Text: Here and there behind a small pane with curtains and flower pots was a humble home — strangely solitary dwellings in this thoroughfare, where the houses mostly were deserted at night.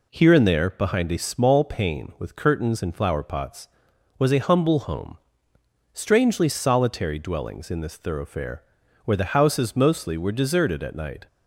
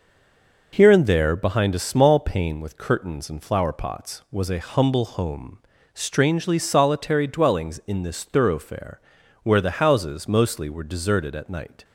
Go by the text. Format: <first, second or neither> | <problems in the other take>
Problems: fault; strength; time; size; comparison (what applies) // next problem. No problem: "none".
first | stays silent before the first word; slight; until 0.7 s; 0.7 s long